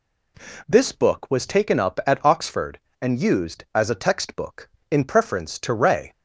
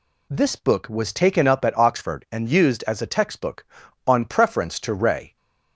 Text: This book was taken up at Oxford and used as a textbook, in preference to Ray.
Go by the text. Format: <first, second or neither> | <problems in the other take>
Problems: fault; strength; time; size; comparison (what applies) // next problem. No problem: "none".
first | says "on" for "in"; at 4.0 s